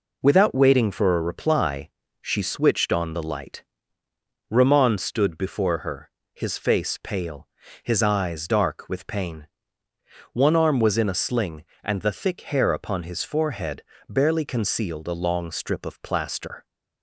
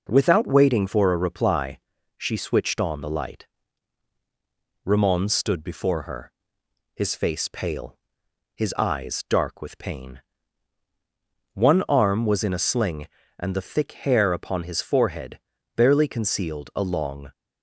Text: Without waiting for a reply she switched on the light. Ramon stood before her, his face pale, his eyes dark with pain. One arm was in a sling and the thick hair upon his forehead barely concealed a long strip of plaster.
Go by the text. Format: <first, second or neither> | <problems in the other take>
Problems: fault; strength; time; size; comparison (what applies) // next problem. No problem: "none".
first | pauses between "reply" and "she"; slight; at 1.7 s; 0.36 s long; slight in the first // pauses between "forehead" and "barely"; slight; at 15.3 s; 0.36 s long; slight in the first // stops before "strip of plaster"; at 17.3 s